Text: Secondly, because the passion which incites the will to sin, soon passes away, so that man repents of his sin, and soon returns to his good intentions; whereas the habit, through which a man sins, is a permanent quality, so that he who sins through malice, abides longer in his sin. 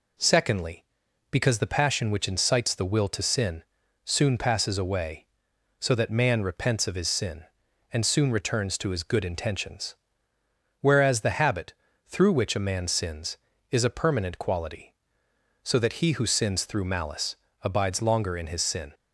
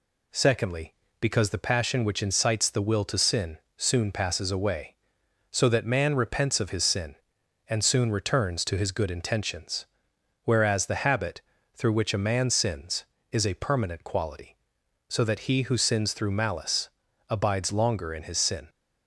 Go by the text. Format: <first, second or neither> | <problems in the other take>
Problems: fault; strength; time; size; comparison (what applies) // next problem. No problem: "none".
neither | none